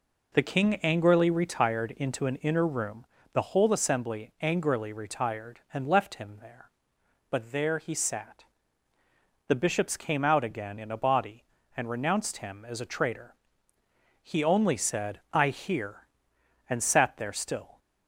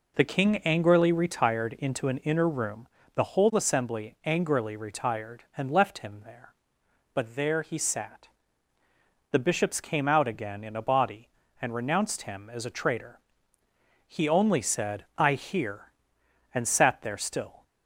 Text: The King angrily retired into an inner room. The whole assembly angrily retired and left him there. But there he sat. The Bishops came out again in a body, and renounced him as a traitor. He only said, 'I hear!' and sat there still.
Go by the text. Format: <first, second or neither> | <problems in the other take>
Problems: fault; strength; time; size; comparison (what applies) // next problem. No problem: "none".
neither | none